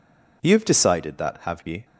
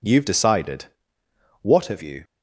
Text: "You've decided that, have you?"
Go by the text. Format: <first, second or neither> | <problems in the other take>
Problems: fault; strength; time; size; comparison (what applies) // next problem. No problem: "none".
first | says "what" for "that"; at 1.6 s